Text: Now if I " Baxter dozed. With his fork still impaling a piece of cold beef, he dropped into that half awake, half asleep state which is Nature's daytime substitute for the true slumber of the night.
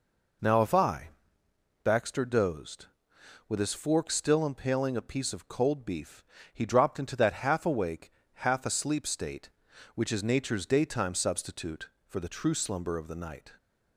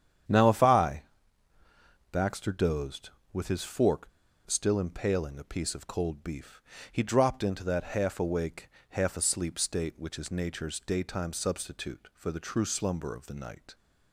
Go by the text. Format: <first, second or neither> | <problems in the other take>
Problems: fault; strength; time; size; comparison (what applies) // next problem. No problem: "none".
first | starts louder than the rest; strong; until 1.8 s; 8.5 dB // pauses between "fork" and "still"; at 4.0 s; 0.38 s long